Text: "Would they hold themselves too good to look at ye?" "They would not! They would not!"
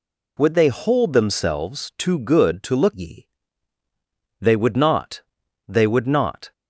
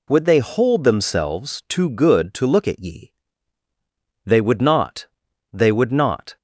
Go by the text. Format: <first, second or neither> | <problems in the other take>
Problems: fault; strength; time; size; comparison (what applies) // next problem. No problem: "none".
second | skips "at"; at 2.9 s